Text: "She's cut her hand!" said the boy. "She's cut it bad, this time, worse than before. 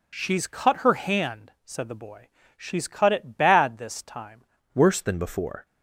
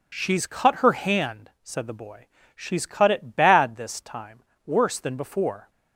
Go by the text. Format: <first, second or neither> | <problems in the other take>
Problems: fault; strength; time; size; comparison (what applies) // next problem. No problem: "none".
second | changes voice at "worse"; from 4.7 s on; 0.9 s long